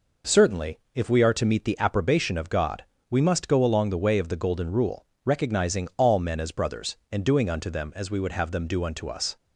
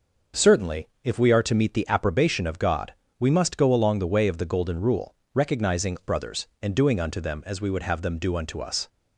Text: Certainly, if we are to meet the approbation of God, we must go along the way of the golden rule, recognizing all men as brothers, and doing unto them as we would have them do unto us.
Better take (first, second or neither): first